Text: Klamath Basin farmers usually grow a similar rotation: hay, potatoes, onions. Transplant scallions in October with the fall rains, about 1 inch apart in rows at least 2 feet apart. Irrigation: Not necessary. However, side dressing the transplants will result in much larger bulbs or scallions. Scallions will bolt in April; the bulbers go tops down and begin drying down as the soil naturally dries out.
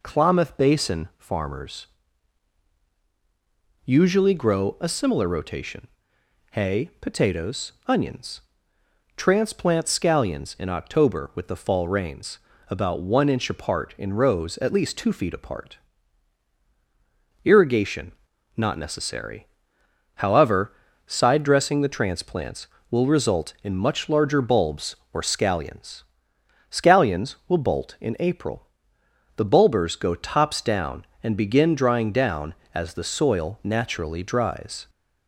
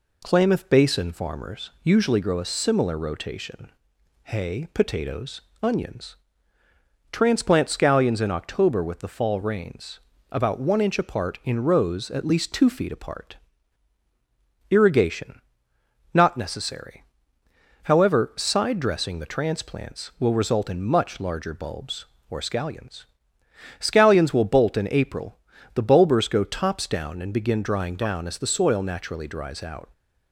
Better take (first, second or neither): second